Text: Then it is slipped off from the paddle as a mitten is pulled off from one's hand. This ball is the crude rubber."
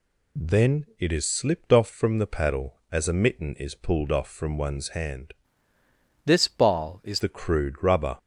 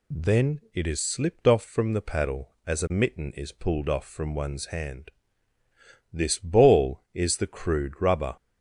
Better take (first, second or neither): second